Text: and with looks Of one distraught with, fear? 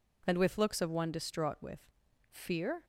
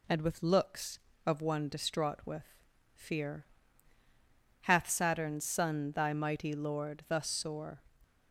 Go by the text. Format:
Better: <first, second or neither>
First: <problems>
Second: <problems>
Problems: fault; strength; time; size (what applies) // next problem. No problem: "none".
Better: first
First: none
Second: goes on to say "hath Saturn's son Thy mighty Lord thus sore"; strong; from 4.6 s on; 3.2 s long